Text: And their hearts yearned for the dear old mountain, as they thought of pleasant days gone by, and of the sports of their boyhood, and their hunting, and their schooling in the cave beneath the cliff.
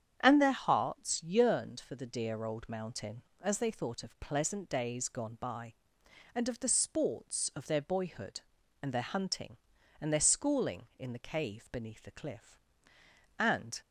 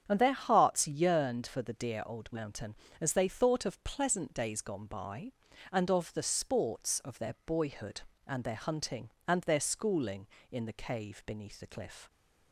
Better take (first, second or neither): second